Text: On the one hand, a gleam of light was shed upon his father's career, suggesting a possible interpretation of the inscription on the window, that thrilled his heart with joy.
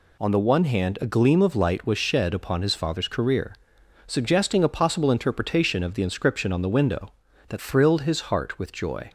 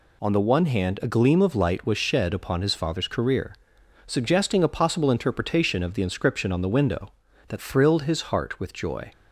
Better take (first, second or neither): neither